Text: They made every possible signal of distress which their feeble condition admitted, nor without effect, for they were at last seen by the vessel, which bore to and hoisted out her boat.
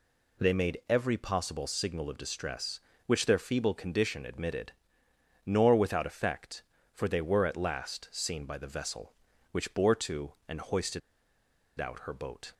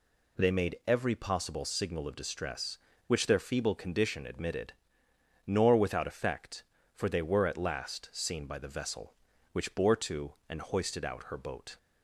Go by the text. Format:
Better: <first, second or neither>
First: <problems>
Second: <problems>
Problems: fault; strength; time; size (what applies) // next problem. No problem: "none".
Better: second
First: pauses between "hoisted" and "out"; noticeable; at 11.0 s; 0.79 s long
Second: none